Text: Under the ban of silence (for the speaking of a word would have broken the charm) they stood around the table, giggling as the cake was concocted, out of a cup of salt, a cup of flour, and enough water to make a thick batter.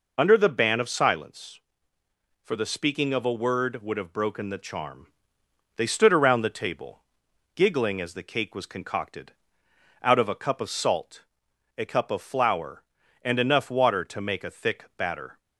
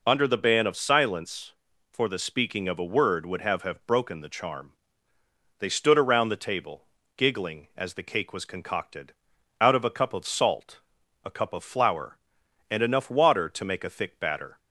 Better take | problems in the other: first | says "have" twice; at 3.6 s

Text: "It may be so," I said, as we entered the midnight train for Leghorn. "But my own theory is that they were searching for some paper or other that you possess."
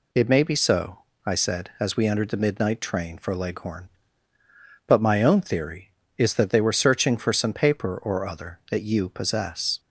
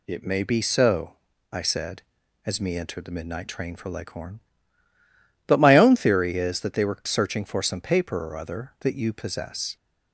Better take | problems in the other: first | says "me" for "we"; at 2.5 s

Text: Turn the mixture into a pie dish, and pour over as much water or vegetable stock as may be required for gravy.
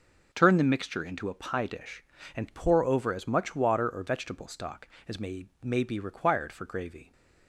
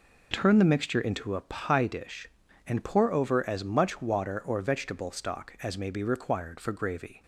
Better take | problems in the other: second | says "may" twice; at 5.6 s

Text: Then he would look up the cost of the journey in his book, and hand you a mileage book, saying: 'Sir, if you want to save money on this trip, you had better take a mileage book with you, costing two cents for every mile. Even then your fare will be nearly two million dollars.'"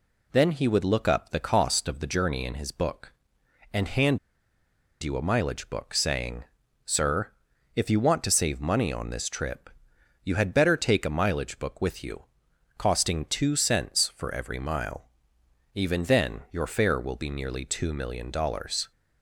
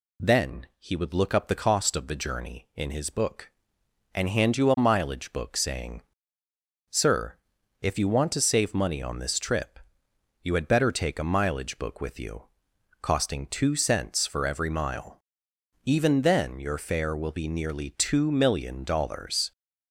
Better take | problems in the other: second | pauses between "hand" and "you"; noticeable; at 4.1 s; 0.84 s long

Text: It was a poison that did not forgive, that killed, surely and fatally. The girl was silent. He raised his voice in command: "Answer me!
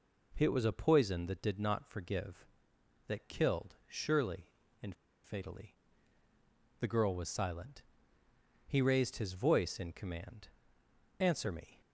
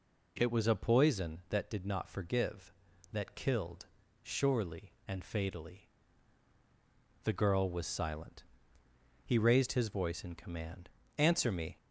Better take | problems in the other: second | pauses between "and" and "fatally"; slight; at 4.9 s; 0.29 s long

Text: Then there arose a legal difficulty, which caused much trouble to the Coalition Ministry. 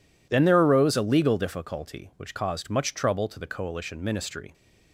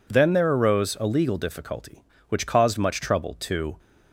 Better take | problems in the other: first | stops before "the Coalition Ministry"; at 3.7 s

